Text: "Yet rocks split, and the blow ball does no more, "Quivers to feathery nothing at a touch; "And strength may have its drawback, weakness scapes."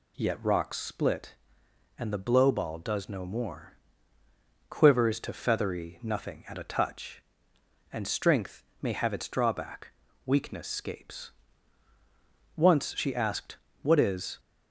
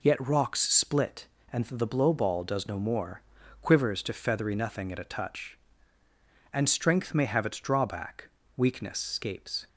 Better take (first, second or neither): second